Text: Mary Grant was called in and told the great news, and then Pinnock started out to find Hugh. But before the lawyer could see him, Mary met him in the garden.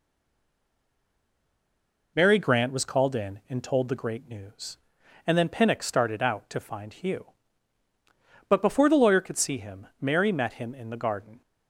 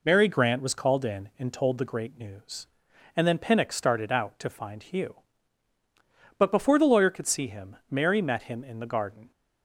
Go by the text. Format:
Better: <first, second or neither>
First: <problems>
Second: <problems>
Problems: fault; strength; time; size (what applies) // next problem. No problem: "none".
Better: second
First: stays silent before the first word; until 2.1 s; 2.1 s long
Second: none